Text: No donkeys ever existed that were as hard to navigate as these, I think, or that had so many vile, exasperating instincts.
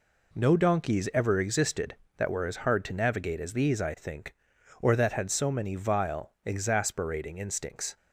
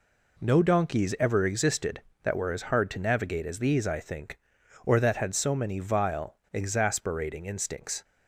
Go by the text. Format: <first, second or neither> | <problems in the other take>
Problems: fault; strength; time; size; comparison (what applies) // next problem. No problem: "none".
neither | none